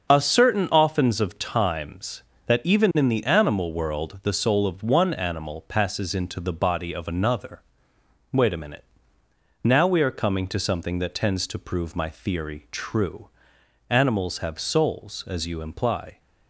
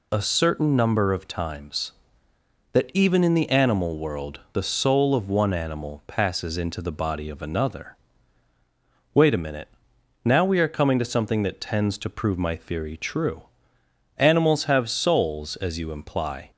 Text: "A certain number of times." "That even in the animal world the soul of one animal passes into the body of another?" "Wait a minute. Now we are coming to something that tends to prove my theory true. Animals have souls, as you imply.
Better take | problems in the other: second | starts louder than the rest; until 1.1 s; 6.5 dB // says "oftens" for "number"; at 0.6 s

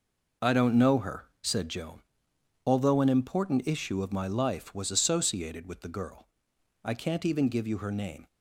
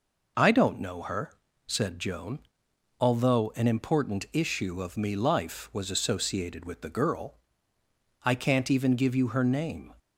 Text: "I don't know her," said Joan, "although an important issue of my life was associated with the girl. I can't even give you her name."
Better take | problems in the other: first | says "me" for "my"; at 4.9 s

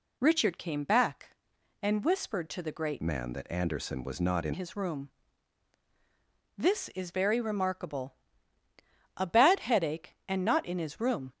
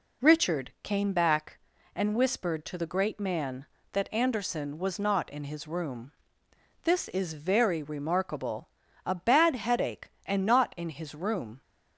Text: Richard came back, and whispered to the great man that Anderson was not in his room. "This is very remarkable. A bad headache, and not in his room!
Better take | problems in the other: second | changes voice from "man" to "in"; from 3.0 to 4.5 s; 1.5 s long

